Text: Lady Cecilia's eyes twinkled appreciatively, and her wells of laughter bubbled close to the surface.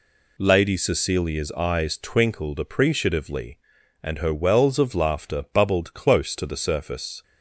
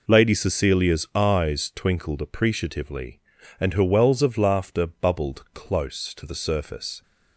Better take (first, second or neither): neither